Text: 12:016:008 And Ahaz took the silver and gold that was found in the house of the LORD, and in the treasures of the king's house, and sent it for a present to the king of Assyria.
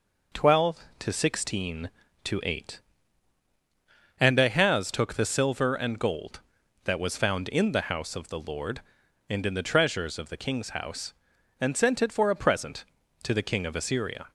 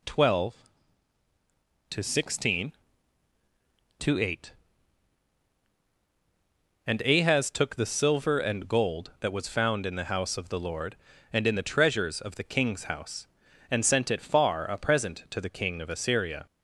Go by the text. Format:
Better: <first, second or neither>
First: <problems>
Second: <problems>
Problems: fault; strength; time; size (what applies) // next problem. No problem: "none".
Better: first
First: none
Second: says "far" for "for"; at 14.1 s